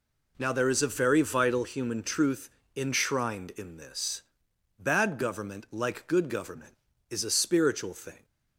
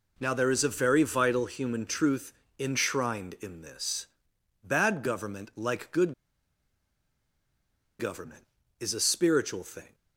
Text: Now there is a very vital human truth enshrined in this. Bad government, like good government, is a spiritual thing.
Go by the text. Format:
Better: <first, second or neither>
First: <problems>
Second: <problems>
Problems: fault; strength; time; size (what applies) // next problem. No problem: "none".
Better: first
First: pauses between "truth" and "enshrined"; slight; at 2.5 s; 0.24 s long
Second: pauses between "truth" and "enshrined"; slight; at 2.3 s; 0.24 s long // pauses between "good" and "government"; strong; at 6.1 s; 1.8 s long